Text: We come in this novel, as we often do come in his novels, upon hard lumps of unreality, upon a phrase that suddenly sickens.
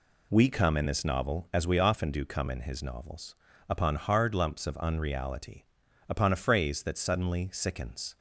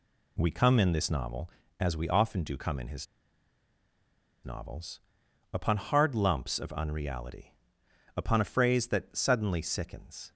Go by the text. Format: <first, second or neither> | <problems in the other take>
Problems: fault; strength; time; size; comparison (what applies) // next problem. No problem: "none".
first | pauses between "his" and "novels"; strong; at 3.0 s; 1.3 s long